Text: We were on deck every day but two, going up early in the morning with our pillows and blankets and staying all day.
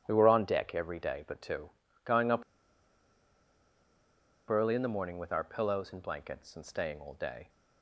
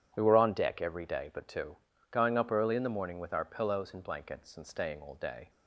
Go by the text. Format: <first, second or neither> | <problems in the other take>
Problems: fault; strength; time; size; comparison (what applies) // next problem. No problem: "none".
second | starts louder than the rest; strong; until 1.0 s; 10 dB // pauses between "up" and "early"; strong; at 2.4 s; 2.0 s long